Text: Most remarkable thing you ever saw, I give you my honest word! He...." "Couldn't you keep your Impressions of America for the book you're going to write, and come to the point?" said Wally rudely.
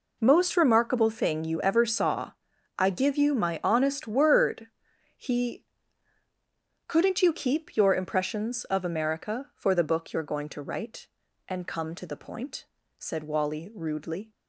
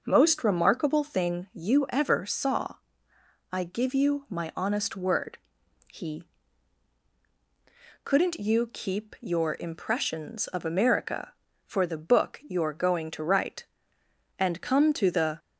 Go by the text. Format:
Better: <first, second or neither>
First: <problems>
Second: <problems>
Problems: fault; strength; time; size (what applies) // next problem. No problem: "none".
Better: first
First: none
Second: stops before "point said Wally rudely"; at 15.3 s